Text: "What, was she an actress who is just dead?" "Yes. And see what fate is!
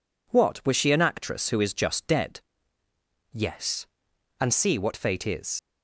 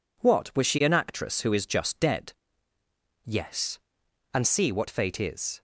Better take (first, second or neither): second